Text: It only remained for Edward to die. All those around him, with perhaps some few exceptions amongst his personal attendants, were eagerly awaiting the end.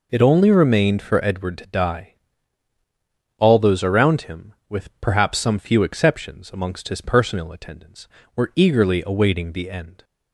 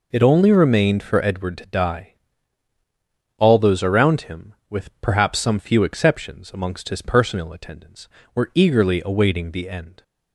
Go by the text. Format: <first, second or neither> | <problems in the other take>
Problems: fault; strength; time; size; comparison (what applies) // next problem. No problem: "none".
neither | none